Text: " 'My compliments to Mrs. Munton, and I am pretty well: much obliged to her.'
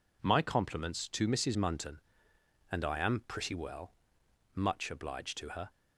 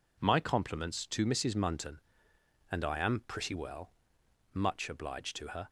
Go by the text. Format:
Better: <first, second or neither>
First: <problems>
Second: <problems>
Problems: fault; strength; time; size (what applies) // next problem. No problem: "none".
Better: neither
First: none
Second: none